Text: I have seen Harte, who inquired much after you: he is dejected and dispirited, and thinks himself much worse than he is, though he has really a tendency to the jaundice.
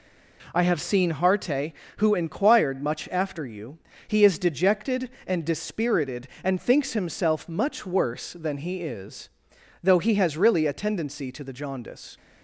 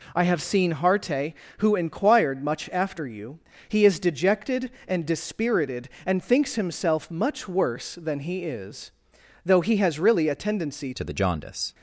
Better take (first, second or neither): first